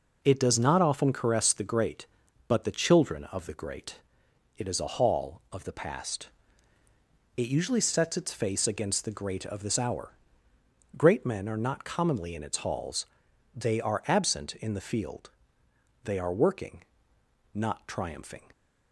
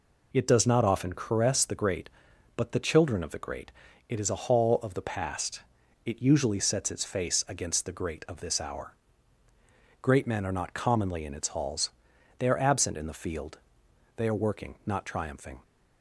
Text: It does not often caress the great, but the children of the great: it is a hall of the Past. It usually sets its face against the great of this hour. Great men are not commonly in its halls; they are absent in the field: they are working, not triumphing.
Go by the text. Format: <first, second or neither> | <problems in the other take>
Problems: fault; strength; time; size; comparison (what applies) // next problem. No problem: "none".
neither | none